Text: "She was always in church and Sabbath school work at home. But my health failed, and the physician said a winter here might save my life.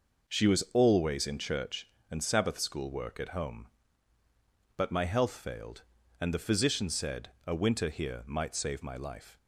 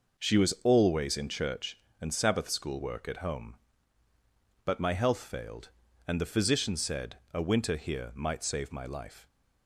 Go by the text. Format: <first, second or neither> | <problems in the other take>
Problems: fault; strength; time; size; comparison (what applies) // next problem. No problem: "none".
neither | pauses between "said" and "a"; slight; the same in both